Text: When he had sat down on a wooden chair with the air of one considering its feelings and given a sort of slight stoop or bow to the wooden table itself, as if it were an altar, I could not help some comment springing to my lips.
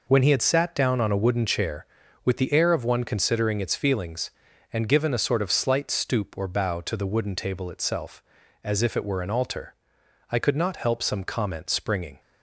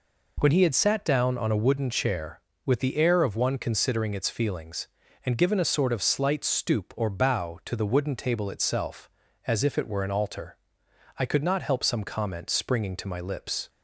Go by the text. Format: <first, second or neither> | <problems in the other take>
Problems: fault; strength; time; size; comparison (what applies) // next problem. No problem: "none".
second | stops before "to my lips"; at 12.1 s